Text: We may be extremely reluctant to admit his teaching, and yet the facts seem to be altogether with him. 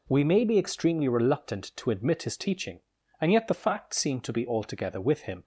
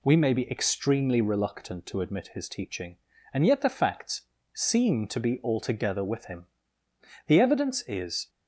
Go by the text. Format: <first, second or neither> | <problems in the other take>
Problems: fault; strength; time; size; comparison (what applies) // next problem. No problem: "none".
first | pauses between "facts" and "seem"; slight; at 4.2 s; 0.32 s long // goes on to say "The evidence is"; noticeable; from 7.2 s on; 1.0 s long